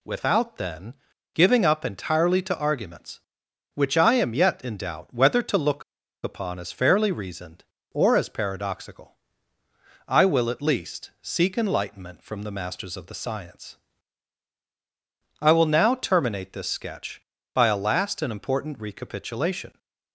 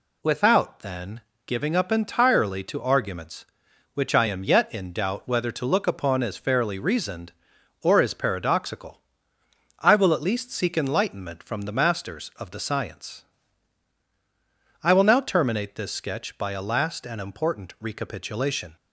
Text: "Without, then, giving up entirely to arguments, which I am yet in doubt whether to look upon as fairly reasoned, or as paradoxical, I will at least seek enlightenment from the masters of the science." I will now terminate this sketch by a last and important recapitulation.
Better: second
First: pauses between "look" and "upon"; at 5.8 s; 0.41 s long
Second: none

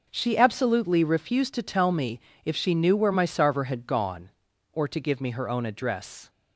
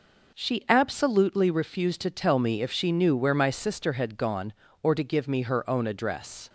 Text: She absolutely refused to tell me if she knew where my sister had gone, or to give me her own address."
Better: second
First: pauses between "me" and "if"; slight; at 2.1 s; 0.24 s long // says "sarver" for "sister"; at 3.2 s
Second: none

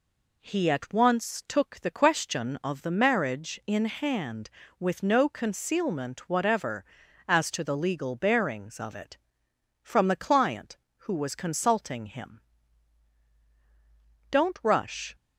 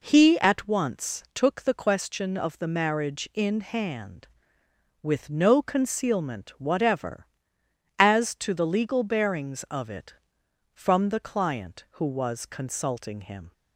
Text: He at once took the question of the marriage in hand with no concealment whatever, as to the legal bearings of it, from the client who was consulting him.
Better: second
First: goes on to say "Don't rush"; noticeable; from 14.3 s on; 0.84 s long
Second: none

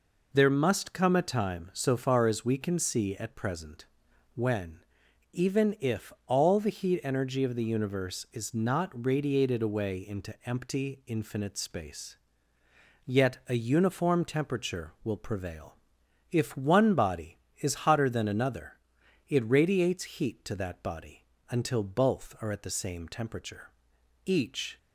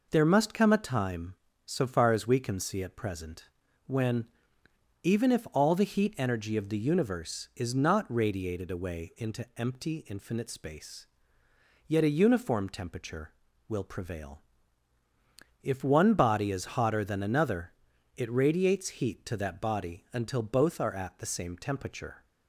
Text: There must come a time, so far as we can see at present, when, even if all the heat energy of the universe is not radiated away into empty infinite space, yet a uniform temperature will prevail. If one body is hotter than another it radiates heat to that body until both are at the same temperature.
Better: second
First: pauses between "another" and "it"; noticeable; at 18.7 s; 0.54 s long // pauses between "body" and "until"; slight; at 21.2 s; 0.26 s long // goes on to say "Each"; from 24.2 s on; 0.52 s long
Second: pauses between "another" and "it"; at 17.7 s; 0.44 s long

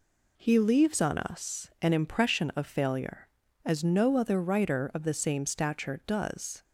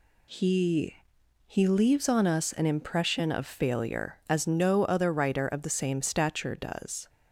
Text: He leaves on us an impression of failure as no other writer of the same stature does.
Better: first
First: none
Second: says "He" twice; at 1.4 s

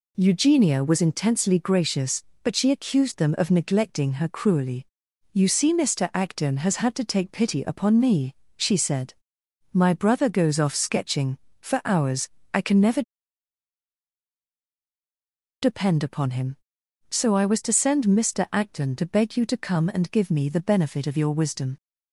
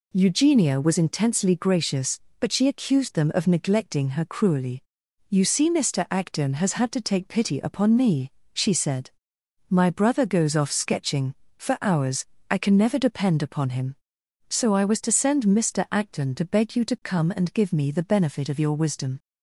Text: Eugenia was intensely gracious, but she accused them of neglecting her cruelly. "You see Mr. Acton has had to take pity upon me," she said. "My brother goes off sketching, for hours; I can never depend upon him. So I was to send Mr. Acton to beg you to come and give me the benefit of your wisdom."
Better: second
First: pauses between "never" and "depend"; strong; at 13.0 s; 2.5 s long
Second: none

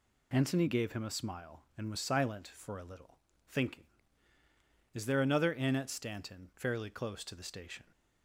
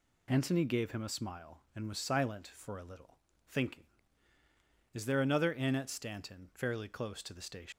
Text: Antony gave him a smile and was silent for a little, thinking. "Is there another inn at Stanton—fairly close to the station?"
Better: first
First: none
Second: leaves "station" unfinished; at 7.7 s; 170 ms

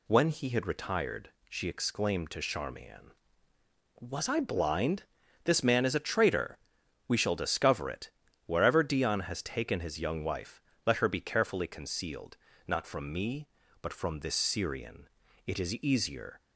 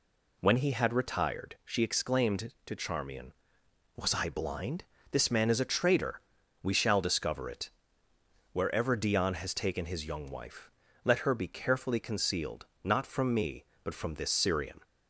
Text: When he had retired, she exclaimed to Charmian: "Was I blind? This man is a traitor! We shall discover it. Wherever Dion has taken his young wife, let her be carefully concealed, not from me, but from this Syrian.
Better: second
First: goes on to say "It is easier"; noticeable; from 15.4 s on; 0.92 s long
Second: none

